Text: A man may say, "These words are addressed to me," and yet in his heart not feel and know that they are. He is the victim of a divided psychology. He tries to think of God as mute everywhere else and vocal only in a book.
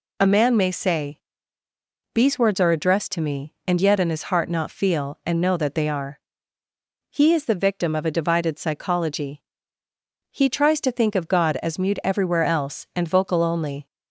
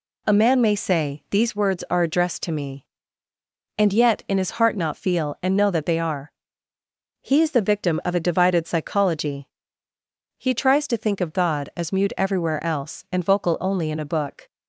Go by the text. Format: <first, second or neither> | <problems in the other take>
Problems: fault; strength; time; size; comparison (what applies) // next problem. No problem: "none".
second | stops before "in a book"; at 13.8 s